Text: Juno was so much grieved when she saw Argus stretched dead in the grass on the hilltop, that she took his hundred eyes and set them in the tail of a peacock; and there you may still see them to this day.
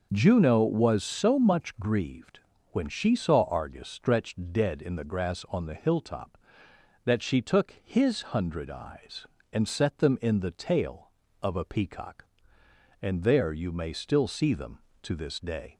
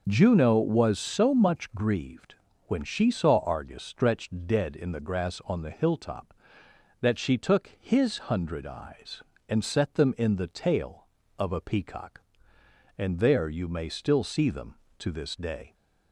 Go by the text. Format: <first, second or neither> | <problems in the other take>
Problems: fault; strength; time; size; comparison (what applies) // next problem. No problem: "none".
neither | pauses between "grieved" and "when"; slight; the same in both